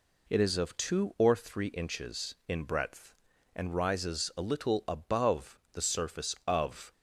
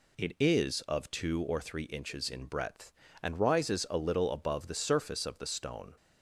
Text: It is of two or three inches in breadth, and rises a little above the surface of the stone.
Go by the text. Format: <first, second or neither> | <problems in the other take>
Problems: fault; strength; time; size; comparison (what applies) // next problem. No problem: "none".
second | stops before "the stone"; at 6.9 s